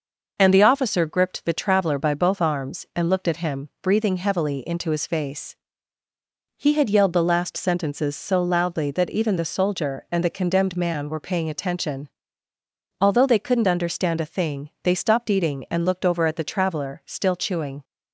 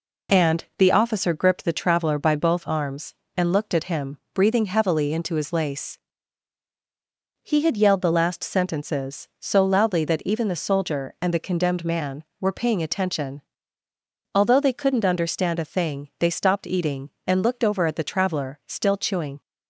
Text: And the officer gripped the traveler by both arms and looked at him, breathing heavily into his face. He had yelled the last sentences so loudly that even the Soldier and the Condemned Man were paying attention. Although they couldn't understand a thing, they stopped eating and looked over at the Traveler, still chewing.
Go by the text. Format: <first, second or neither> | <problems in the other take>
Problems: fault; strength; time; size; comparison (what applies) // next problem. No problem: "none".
first | pauses between "And" and "the"; slight; at 0.6 s; 0.16 s long // says "lace" for "face"; at 5.5 s